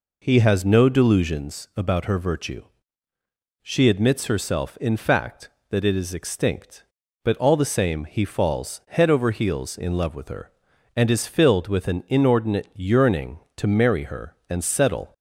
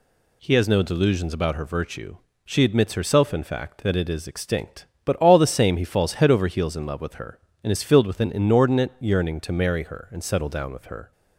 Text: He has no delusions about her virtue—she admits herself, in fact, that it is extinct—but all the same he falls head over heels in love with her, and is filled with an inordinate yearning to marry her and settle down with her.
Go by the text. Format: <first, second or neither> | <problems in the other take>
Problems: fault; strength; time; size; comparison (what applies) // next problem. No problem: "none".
second | stops before "down with her"; at 15.1 s